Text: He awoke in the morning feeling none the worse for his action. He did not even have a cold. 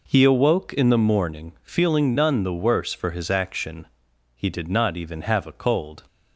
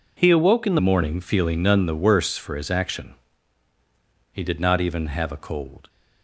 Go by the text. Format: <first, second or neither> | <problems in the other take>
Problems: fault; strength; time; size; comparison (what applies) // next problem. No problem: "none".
first | changes voice at "morning"; from 0.8 s on; 5.0 s long